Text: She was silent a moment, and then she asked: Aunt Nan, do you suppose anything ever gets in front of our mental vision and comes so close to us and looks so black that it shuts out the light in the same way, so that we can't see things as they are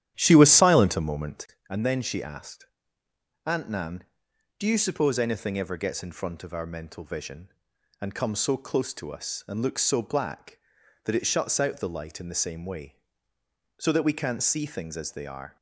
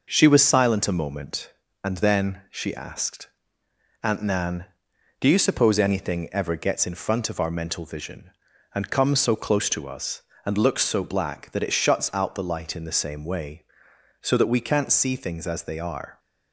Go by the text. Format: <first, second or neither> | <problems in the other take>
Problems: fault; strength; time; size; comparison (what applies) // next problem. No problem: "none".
second | starts louder than the rest; strong; until 1.6 s; 11 dB